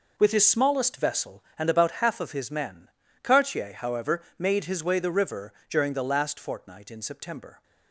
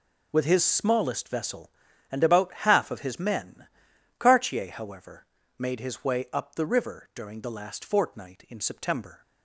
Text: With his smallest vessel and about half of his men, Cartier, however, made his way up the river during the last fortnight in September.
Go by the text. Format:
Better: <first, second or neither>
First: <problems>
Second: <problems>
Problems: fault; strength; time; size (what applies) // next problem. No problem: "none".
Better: second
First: skips "up"; at 4.9 s // pauses between "river" and "during"; slight; at 5.5 s; 0.16 s long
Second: none